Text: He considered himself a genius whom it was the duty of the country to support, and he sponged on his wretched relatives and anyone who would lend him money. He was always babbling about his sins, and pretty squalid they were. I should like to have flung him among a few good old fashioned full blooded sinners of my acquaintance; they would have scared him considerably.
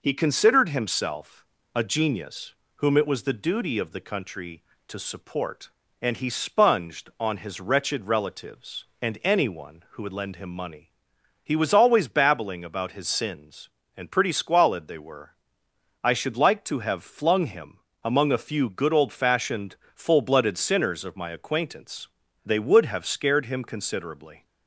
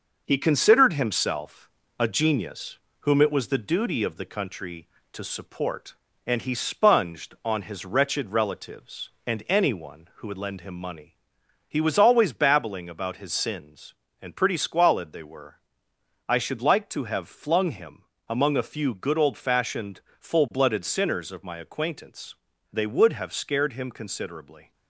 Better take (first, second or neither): first